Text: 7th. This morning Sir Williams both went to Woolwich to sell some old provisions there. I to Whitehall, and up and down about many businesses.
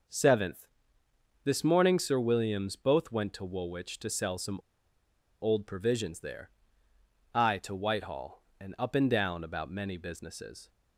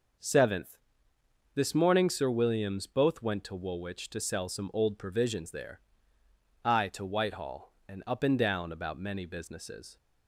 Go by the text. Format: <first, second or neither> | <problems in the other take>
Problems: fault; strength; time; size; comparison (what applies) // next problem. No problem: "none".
second | pauses between "some" and "old"; noticeable; at 4.5 s; 0.84 s long